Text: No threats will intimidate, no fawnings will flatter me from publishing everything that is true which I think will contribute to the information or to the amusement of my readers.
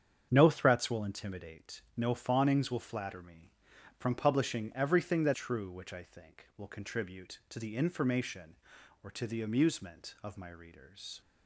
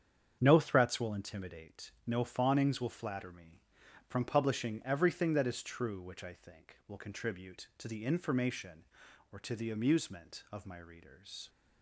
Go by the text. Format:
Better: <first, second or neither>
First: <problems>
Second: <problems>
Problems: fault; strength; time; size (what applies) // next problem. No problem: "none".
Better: second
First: starts louder than the rest; strong; until 1.3 s; 8 dB // skips "is"; at 5.3 s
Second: starts louder than the rest; strong; until 1.4 s; 8 dB